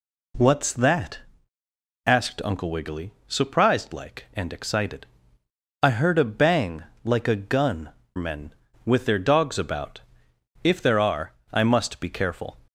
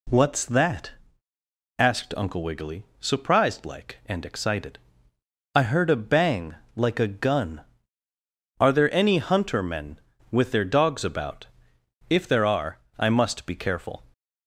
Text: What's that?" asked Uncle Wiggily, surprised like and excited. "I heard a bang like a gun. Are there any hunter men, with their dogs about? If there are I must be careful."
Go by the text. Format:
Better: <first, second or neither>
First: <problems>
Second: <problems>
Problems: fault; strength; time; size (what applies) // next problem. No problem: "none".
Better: second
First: pauses between "bang" and "like"; slight; at 6.8 s; 0.22 s long // skips "Are there any hunter"; at 8.0 s // pauses between "are" and "I"; slight; at 11.3 s; 0.20 s long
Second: pauses between "bang" and "like"; slight; at 6.5 s; 0.22 s long // pauses between "are" and "I"; slight; at 12.7 s; 0.20 s long